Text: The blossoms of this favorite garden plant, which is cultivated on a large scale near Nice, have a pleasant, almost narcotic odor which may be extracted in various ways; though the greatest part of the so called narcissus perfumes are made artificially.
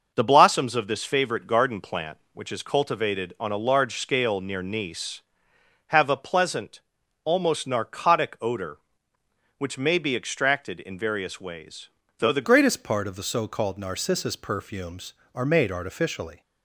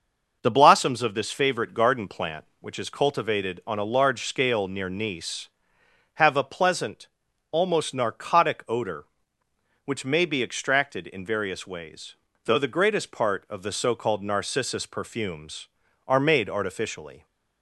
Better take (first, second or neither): second